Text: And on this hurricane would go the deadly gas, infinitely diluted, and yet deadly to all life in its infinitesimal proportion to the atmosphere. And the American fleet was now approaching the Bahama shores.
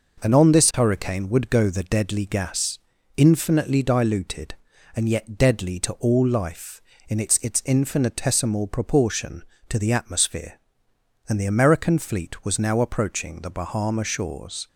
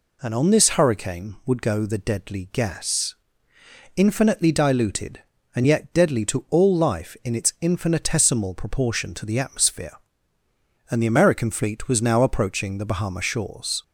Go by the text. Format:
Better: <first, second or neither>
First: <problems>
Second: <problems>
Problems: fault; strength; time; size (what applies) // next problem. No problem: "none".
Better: second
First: says "its" twice; at 7.3 s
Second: none